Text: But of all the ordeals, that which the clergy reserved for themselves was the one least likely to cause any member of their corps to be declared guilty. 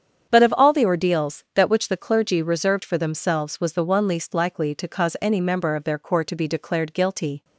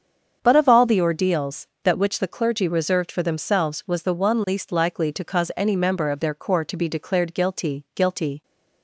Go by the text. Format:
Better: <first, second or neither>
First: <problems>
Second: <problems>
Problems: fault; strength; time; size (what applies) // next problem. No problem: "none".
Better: first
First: starts louder than the rest; strong; until 1.3 s; 8 dB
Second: starts louder than the rest; strong; until 1.4 s; 7.5 dB // says "guilty" twice; at 7.9 s